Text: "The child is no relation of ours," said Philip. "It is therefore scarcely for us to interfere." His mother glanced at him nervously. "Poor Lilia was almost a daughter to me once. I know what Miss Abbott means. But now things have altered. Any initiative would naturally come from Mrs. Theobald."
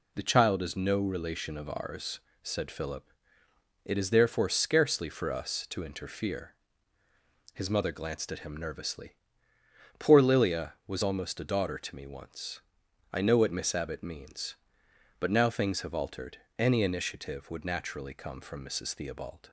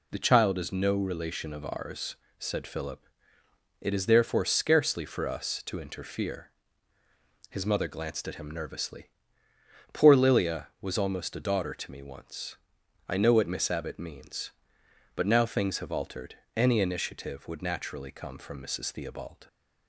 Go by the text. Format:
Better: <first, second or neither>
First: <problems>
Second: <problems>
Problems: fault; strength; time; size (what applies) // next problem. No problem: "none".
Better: neither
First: none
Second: none